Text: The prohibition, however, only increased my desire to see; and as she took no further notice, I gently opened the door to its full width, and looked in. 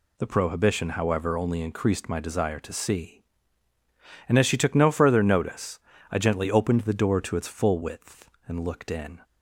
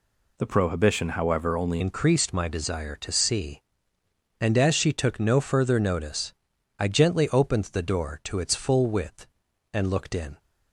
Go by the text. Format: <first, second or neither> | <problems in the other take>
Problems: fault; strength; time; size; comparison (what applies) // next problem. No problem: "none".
first | changes voice at "increased"; from 1.8 s on; 8.5 s long